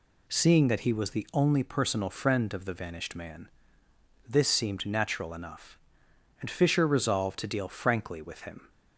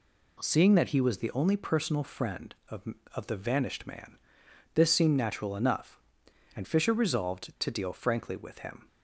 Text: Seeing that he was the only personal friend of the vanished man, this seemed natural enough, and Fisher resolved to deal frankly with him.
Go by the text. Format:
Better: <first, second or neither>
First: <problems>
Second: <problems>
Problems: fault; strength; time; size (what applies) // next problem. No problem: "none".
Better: first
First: none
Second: says "of" twice; at 3.1 s